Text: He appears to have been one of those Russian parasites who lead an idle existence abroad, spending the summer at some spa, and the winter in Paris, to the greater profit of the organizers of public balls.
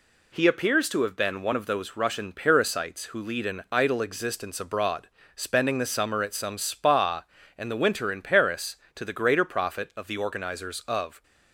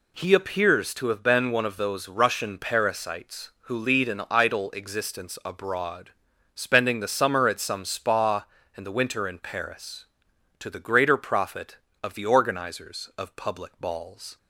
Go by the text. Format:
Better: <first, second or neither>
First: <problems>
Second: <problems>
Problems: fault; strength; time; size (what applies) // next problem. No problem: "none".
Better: second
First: stops before "public balls"; at 11.2 s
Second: none